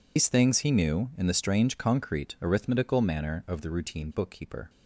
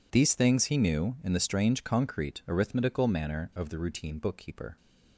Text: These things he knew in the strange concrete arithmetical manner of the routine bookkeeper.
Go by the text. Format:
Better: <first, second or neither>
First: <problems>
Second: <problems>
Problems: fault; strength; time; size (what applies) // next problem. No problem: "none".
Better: second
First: loses the start of "These"; at 0.1 s; 100 ms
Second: none